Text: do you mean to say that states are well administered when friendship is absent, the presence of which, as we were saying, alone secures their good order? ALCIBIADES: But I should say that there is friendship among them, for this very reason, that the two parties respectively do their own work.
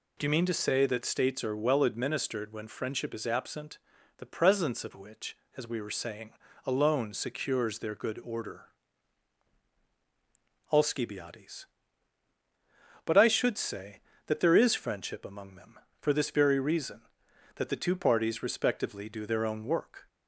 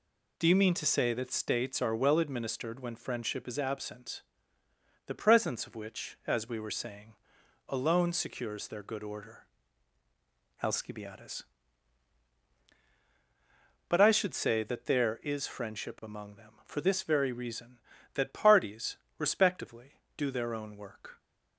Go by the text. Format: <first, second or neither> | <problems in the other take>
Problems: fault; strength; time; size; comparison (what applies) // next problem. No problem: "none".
first | skips "the two"; at 18.3 s // pauses between "parties" and "respectively"; slight; at 18.9 s; 0.22 s long